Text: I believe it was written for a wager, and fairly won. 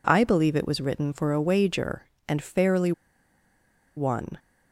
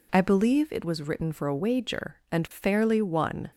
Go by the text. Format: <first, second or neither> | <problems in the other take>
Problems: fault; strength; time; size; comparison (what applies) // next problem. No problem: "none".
second | pauses between "fairly" and "won"; at 2.9 s; 1.0 s long